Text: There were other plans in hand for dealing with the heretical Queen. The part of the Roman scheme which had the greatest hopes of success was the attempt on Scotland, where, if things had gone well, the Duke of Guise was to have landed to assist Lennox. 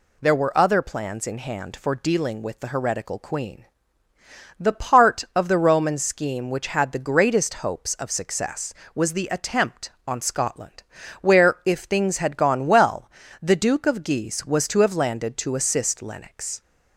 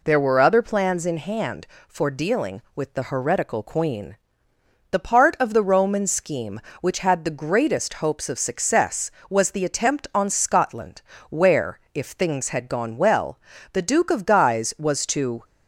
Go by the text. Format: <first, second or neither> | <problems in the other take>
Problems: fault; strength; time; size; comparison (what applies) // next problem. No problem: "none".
first | stops before "have landed to assist Lennox"; at 15.4 s